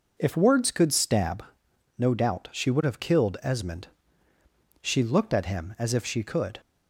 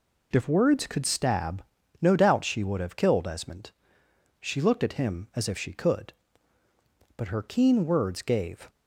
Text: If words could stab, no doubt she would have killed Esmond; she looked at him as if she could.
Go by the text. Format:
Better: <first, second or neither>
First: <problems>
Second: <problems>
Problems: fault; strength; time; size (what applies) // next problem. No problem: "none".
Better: first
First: none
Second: goes on to say "But her keen words gave"; from 7.1 s on; 1.5 s long